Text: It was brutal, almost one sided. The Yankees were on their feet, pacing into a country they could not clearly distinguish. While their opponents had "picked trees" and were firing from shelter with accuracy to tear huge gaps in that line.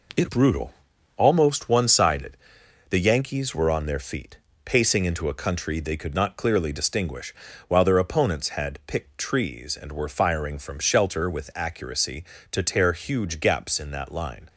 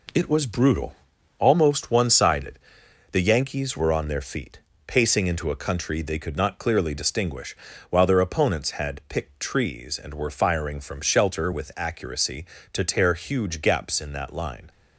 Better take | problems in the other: second | skips "was"; at 0.2 s

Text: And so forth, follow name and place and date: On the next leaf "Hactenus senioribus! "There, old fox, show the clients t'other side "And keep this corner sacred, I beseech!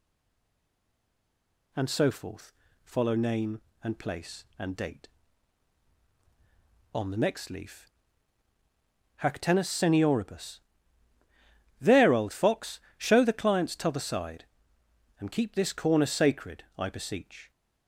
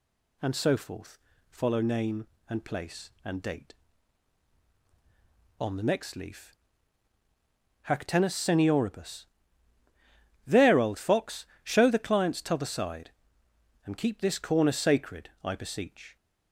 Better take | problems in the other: second | stays silent before the first word; noticeable; until 1.7 s; 1.7 s long // pauses between "leaf" and "Hactenus"; strong; at 7.8 s; 1.3 s long; strong in the second

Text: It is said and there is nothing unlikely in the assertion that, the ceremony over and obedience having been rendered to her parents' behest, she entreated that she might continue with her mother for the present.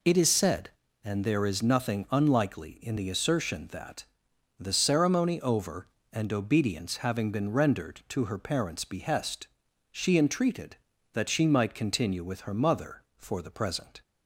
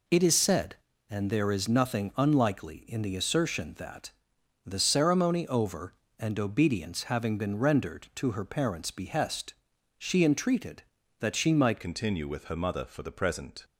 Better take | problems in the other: first | changes voice at "continue"; from 11.8 s on; 1.8 s long

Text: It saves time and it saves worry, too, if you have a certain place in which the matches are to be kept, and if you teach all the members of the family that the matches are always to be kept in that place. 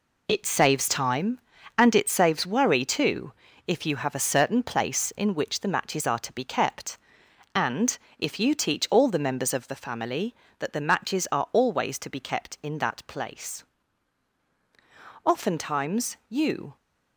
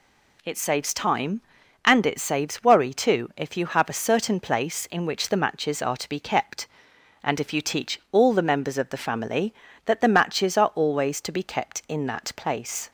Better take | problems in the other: second | pauses between "and" and "if"; slight; at 7.9 s; 0.20 s long // goes on to say "Oftentimes you"; from 15.2 s on; 1.5 s long

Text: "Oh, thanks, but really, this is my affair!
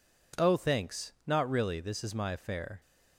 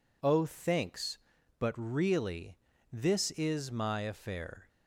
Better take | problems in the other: second | says "not" for "but"; at 1.2 s

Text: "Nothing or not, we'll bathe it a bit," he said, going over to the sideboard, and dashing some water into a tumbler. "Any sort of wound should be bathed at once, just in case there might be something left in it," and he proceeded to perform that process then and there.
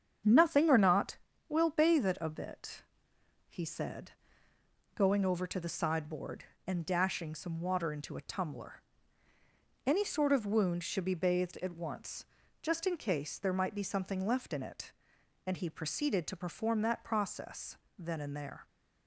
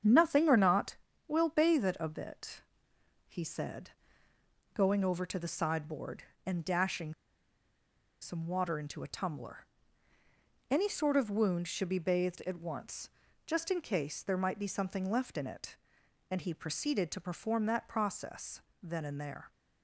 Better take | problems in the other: first | starts louder than the rest; strong; until 1.3 s; 8 dB; strong in the first // pauses between "dashing" and "some"; at 7.1 s; 1.0 s long // pauses between "process" and "then"; slight; at 18.6 s; 0.20 s long; slight in the first

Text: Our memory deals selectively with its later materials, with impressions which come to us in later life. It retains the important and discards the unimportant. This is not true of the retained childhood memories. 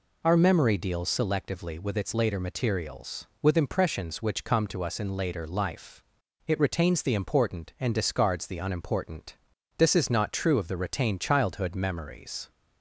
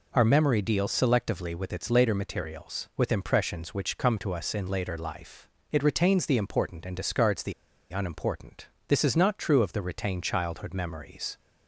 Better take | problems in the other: first | pauses between "the" and "unimportant"; at 7.5 s; 0.38 s long

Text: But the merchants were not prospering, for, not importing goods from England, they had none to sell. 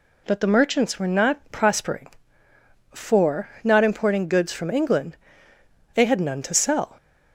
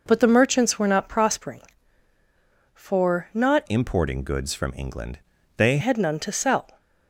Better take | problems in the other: first | changes voice from "importing" to "they"; from 3.6 to 5.7 s; 2.1 s long

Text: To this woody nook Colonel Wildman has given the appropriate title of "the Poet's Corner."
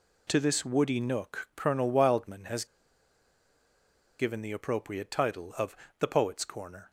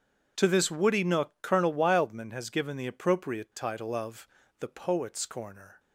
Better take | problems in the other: second | pauses between "has" and "given"; strong; at 2.6 s; 1.5 s long // pauses between "of" and "the"; slight; at 5.7 s; 0.26 s long; slight in the second

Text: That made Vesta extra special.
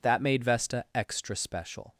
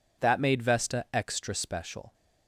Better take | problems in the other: neither | none

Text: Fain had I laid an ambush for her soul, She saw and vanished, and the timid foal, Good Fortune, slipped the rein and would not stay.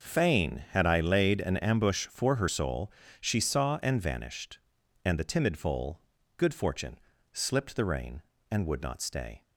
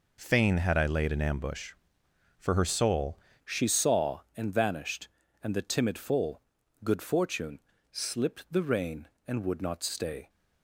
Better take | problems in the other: first | changes voice at "She"; from 3.4 s on; 6.8 s long

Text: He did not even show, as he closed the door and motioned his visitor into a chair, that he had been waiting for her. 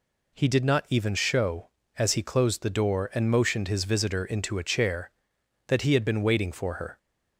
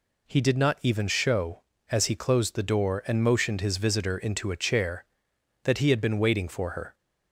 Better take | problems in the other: neither | none

